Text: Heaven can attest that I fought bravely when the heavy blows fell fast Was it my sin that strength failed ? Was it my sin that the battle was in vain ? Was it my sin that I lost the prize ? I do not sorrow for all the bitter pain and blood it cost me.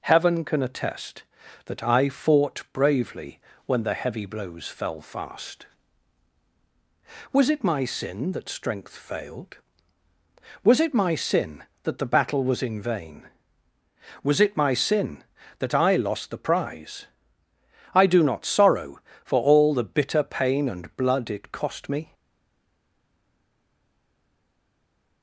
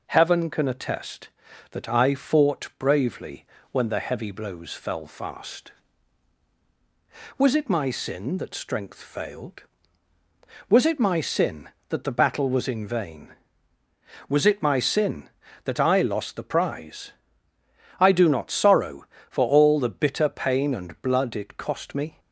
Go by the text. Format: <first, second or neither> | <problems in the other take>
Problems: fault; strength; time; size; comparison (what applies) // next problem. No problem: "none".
second | pauses between "bravely" and "when"; slight; at 3.3 s; 0.26 s long; slight in the second // stays silent after the last word; strong; from 22.1 s on; 3.1 s long